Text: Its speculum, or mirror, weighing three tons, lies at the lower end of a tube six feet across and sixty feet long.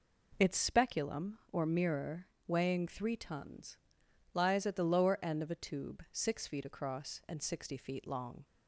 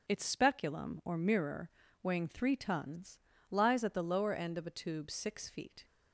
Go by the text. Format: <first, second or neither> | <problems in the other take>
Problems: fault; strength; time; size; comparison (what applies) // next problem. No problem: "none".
first | starts louder than the rest; noticeable; until 1.1 s; 6 dB // stops before "across and sixty feet long"; at 5.8 s